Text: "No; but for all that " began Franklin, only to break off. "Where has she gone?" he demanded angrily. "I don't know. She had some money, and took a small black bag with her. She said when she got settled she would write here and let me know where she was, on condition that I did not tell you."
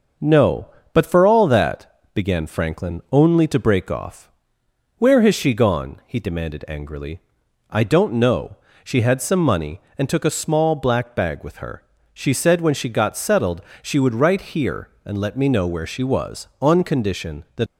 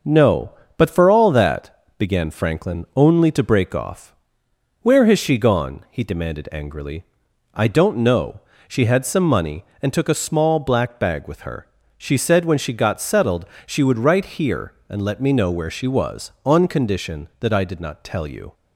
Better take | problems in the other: second | starts louder than the rest; until 1.4 s; 6 dB; also in the second // pauses between "settled" and "she"; slight; at 13.6 s; 0.22 s long; slight in the second // stops before "I did not tell you"; at 17.6 s

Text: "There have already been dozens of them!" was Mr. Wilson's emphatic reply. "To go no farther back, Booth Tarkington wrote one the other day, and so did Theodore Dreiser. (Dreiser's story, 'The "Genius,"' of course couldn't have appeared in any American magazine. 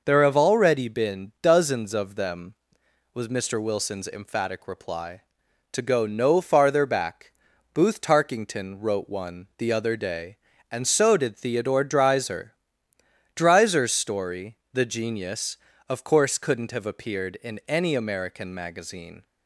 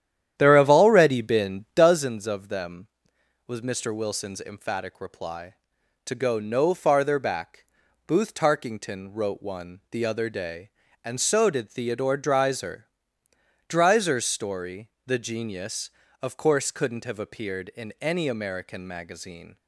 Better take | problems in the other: first | starts louder than the rest; strong; until 2.0 s; 10.5 dB

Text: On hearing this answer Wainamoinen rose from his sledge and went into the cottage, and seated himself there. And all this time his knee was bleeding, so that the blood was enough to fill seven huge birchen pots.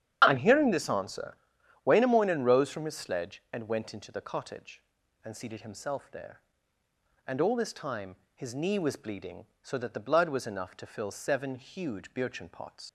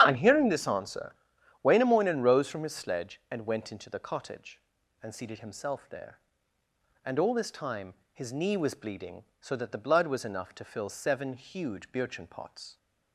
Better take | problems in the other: second | starts louder than the rest; strong; until 1.2 s; 8 dB; strong in the second // pauses between "answer" and "Wainamoinen"; noticeable; at 1.3 s; 0.48 s long; noticeable in the second // pauses between "time" and "his"; slight; at 8.1 s; 0.18 s long; slight in the second // leaves "pots" unfinished; at 12.8 s; 95 ms

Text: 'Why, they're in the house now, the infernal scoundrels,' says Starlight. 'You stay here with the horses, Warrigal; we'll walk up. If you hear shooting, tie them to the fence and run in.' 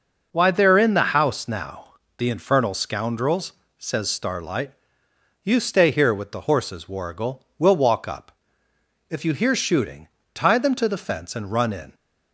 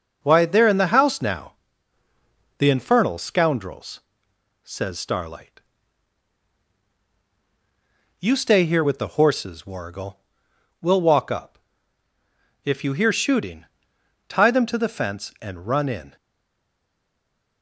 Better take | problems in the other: first | stays silent after the last word; noticeable; from 16.1 s on; 1.5 s long

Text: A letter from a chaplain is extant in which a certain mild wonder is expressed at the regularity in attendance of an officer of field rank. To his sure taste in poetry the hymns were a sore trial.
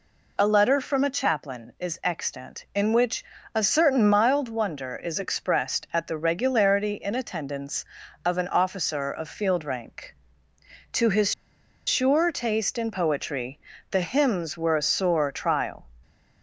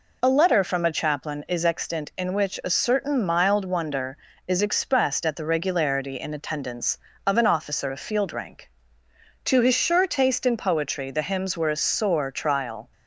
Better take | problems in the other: second | pauses between "which" and "a"; slight; at 3.2 s; 0.30 s long // pauses between "his" and "sure"; noticeable; at 11.3 s; 0.53 s long // pauses between "poetry" and "the"; slight; at 13.5 s; 0.32 s long

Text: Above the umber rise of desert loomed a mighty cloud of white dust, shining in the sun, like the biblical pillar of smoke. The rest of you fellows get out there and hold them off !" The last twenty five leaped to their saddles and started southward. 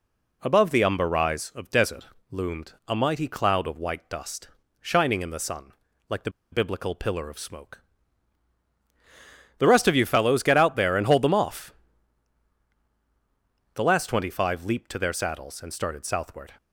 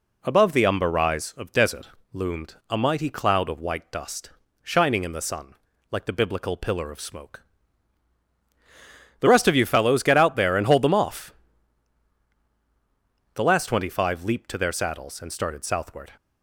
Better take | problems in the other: second | pauses between "desert" and "loomed"; slight; at 2.0 s; 0.26 s long; slight in the second // pauses between "loomed" and "a"; slight; at 2.7 s; 0.16 s long; slight in the second // pauses between "the" and "biblical"; slight; at 6.2 s; 0.22 s long

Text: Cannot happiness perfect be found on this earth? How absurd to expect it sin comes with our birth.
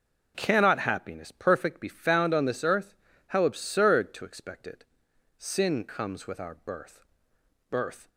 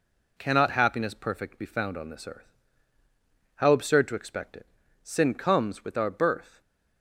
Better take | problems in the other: second | pauses between "it" and "sin"; noticeable; at 4.8 s; 0.54 s long; slight in the second // says "birth" twice; at 7.6 s

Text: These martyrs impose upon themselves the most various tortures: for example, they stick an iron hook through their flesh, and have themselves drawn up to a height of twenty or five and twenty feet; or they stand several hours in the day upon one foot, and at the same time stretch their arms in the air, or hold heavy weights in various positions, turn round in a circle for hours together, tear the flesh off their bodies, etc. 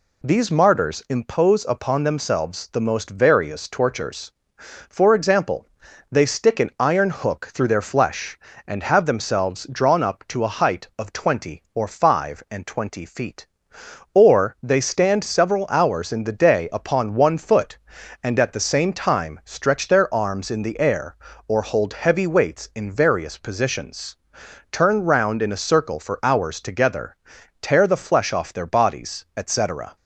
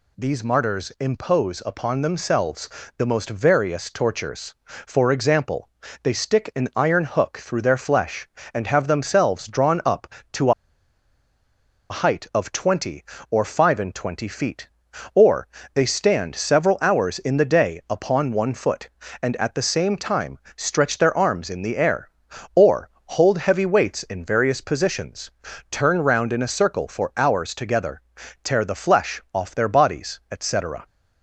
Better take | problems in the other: first | pauses between "themselves" and "the"; slight; at 2.6 s; 0.30 s long // pauses between "to" and "a"; strong; at 10.5 s; 1.3 s long // pauses between "or" and "they"; slight; at 15.4 s; 0.28 s long // pauses between "time" and "stretch"; slight; at 20.3 s; 0.18 s long // pauses between "or" and "hold"; slight; at 22.8 s; 0.20 s long

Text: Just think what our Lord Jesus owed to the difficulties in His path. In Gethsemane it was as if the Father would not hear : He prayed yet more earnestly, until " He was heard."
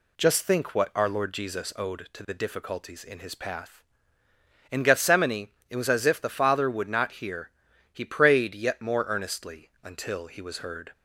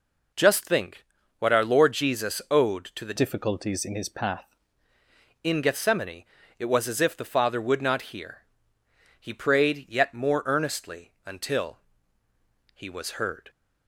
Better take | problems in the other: first | pauses between "think" and "what"; slight; at 1.0 s; 0.34 s long // changes voice from "difficulties" to "path"; from 3.1 to 4.4 s; 1.3 s long // pauses between "Gethsemane" and "it"; slight; at 6.2 s; 0.34 s long; slight in the first

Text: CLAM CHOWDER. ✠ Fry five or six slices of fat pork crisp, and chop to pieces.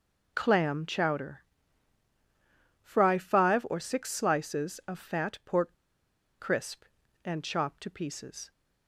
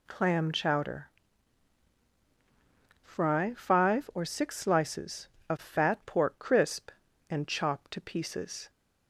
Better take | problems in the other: second | pauses between "pork" and "crisp"; noticeable; at 5.7 s; 0.63 s long

